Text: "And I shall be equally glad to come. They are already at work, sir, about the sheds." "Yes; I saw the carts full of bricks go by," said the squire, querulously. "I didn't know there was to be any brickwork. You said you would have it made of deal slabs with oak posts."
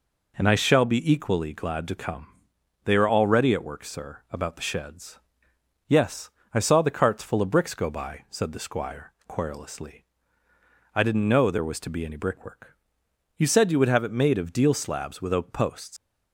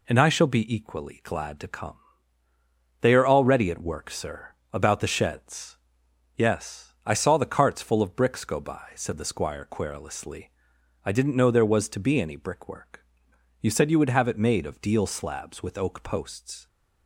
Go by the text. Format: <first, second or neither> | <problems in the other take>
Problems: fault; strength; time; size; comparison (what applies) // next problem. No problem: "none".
second | leaves "posts" unfinished; at 15.9 s; 135 ms